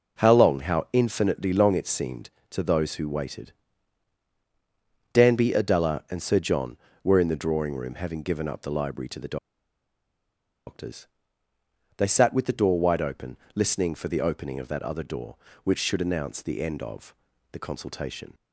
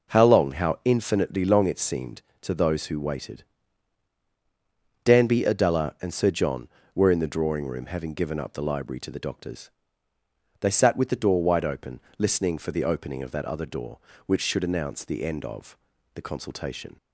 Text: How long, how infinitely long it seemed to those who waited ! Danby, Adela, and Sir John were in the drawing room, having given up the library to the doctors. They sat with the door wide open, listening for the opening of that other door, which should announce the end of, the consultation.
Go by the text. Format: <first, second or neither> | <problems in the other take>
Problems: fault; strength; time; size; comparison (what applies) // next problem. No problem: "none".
second | pauses between "the" and "doctors"; strong; at 9.3 s; 1.3 s long